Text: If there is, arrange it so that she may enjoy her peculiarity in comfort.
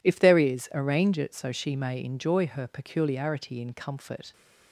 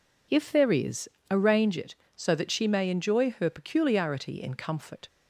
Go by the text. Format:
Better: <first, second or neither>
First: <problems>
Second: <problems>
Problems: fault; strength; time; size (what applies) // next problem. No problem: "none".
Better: second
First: skips "that"; at 1.5 s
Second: none